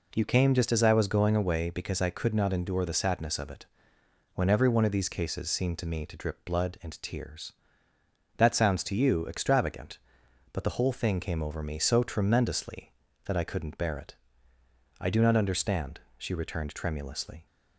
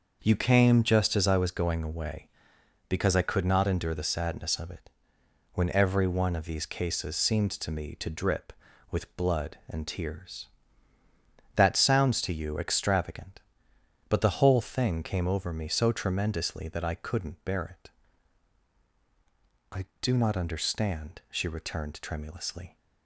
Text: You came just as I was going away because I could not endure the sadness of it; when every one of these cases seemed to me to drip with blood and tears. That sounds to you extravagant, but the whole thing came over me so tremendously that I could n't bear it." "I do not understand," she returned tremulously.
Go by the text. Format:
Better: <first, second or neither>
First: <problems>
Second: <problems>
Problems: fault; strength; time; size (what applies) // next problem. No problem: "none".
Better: second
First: skips "with"; at 6.4 s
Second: none